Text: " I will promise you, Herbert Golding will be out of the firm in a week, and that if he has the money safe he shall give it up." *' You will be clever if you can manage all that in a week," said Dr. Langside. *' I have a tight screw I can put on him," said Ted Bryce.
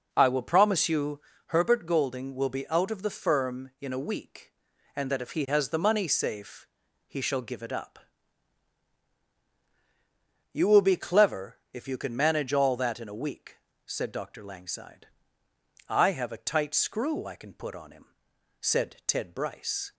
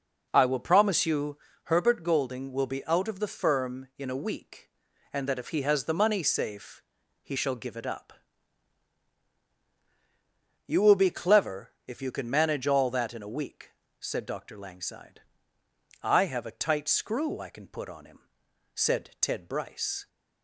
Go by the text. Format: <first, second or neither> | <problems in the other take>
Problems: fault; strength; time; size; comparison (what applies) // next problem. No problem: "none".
neither | starts louder than the rest; strong; the same in both // pauses between "safe" and "he"; the same in both